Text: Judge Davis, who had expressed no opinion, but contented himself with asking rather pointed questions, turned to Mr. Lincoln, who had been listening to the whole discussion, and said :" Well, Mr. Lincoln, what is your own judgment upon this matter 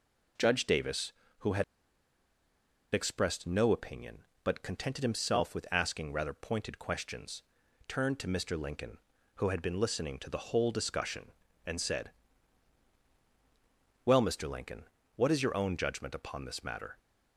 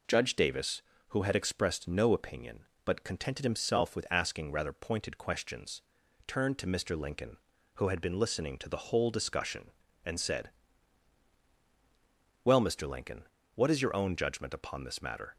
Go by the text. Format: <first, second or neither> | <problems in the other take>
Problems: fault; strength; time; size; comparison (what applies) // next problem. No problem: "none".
second | pauses between "had" and "expressed"; strong; at 1.6 s; 1.2 s long